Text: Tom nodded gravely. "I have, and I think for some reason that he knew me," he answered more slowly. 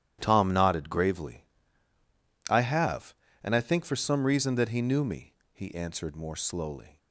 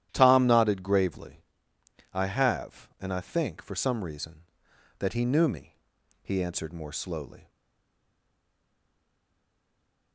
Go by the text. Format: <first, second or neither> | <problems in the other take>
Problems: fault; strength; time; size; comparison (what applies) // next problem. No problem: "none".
first | starts louder than the rest; strong; until 1.1 s; 12 dB; strong in the first // stays silent after the last word; strong; from 7.4 s on; 2.7 s long